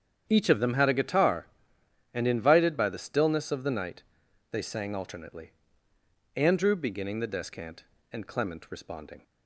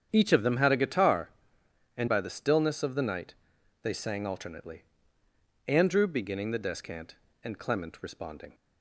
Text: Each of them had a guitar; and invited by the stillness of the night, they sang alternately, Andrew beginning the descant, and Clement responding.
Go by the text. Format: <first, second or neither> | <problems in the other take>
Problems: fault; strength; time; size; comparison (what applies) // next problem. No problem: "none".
first | starts louder than the rest; strong; until 1.1 s; 8 dB; strong in the first // skips "invited"; at 2.0 s